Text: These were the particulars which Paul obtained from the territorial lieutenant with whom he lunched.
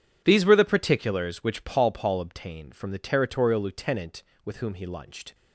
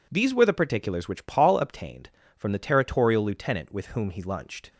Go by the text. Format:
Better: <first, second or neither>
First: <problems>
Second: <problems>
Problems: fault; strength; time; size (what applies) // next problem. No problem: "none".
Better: second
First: says "Paul" twice; at 1.9 s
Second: none